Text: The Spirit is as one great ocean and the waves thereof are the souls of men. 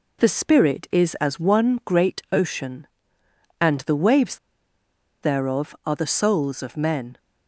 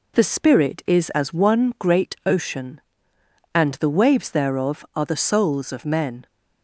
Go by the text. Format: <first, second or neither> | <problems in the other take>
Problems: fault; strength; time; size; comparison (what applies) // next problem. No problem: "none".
second | pauses between "waves" and "thereof"; noticeable; at 4.3 s; 0.87 s long